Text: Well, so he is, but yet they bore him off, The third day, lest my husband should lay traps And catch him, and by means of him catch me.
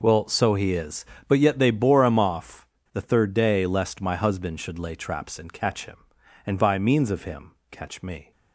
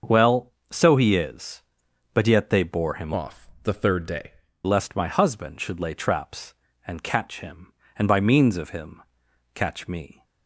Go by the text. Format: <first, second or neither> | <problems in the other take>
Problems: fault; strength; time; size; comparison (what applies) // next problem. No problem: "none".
first | starts louder than the rest; until 1.2 s; 6.5 dB // changes voice from "off" to "day"; from 3.1 to 4.3 s; 1.2 s long // pauses between "him" and "catch"; noticeable; at 9.0 s; 0.54 s long; slight in the first